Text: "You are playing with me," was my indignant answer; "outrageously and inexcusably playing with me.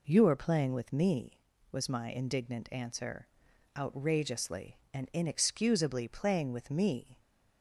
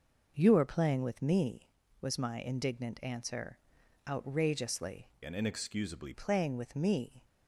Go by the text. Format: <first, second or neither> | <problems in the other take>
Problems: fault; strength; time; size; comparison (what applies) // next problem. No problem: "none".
first | changes voice from "and" to "inexcusably"; from 5.2 to 6.1 s; 0.9 s long